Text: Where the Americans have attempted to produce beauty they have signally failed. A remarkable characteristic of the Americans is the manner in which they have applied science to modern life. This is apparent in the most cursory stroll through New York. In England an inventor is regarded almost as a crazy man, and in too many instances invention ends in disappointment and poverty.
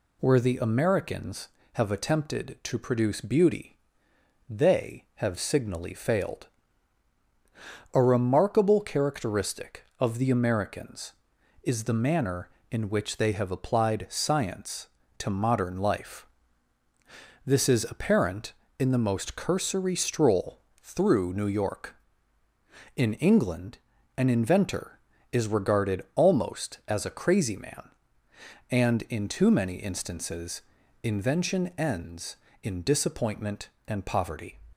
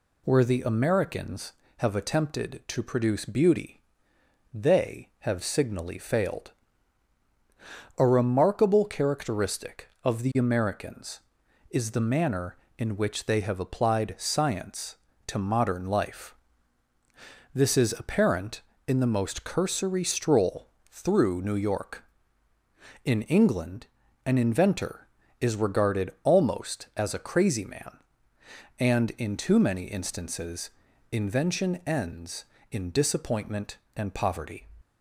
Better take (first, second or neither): neither